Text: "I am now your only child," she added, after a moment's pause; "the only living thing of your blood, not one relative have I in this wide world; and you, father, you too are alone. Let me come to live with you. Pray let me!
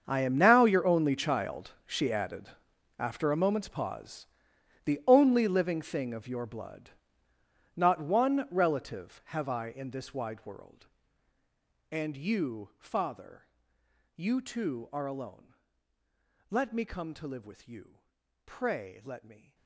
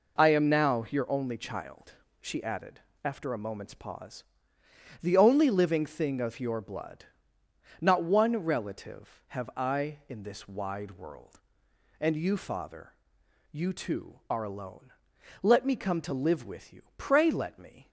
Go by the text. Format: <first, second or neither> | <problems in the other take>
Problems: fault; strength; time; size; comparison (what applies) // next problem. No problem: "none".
second | gets quieter; strong; throughout; 18 dB